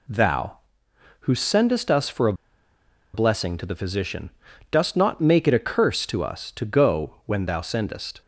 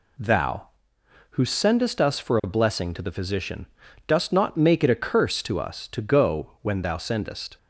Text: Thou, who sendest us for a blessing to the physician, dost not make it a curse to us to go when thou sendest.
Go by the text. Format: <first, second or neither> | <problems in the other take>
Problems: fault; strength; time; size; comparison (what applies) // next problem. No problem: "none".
second | pauses between "a" and "blessing"; noticeable; at 2.3 s; 0.80 s long